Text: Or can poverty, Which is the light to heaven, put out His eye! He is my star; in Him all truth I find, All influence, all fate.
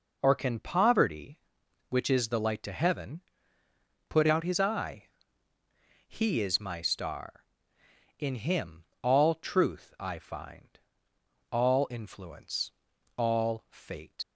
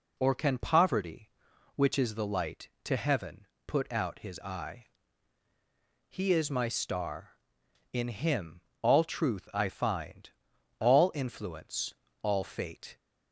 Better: second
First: pauses between "Him" and "all"; slight; at 8.8 s; 0.18 s long // leaves "fate" unfinished; at 14.2 s; 115 ms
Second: pauses between "Him" and "all"; slight; at 8.6 s; 0.20 s long

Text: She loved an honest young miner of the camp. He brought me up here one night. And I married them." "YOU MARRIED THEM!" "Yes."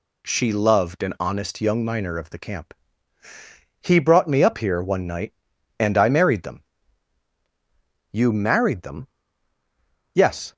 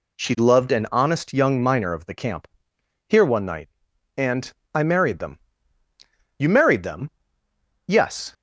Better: first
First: none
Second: skips "He brought me up"; at 2.7 s // pauses between "And" and "I"; slight; at 4.5 s; 0.22 s long

